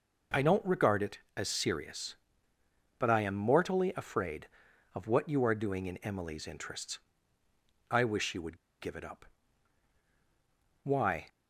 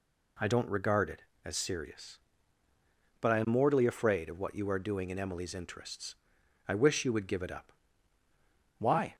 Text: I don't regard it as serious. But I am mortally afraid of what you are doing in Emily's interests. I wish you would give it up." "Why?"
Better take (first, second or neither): second